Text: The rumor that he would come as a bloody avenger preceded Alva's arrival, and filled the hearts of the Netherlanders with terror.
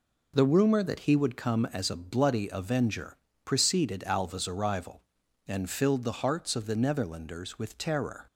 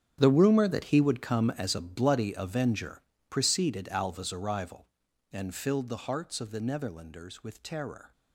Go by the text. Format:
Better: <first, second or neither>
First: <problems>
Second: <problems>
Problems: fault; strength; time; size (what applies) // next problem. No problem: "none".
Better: first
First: pauses between "avenger" and "preceded"; slight; at 3.1 s; 0.28 s long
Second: gets quieter; strong; throughout; 15 dB // pauses between "avenger" and "preceded"; slight; at 3.0 s; 0.28 s long